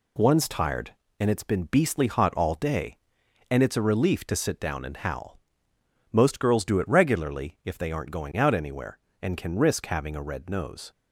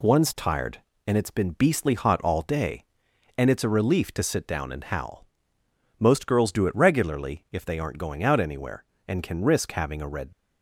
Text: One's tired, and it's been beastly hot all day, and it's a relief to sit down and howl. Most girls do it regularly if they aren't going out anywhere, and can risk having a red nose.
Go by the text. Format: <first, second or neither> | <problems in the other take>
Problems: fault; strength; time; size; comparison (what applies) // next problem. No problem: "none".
first | stops before "nose"; at 10.3 s